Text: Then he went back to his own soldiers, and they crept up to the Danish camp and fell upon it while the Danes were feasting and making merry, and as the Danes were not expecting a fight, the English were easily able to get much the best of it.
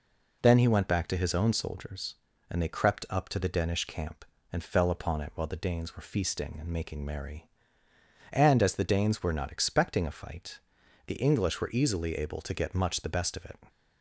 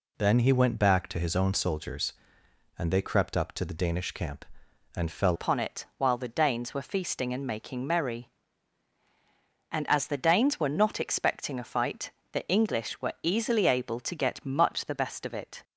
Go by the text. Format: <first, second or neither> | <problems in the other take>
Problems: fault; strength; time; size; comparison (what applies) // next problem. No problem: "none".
first | changes voice at "upon"; from 5.3 s on; 10.3 s long